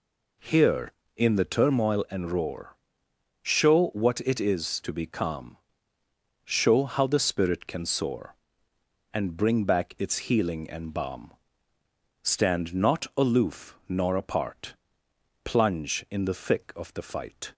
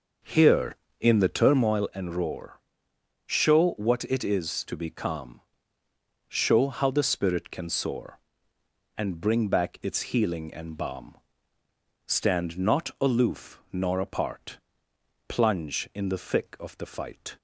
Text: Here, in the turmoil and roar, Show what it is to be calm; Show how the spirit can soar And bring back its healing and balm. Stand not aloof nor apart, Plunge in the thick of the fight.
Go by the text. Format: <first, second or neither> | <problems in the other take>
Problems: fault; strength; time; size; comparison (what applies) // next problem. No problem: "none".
first | starts louder than the rest; noticeable; until 1.8 s; 5.5 dB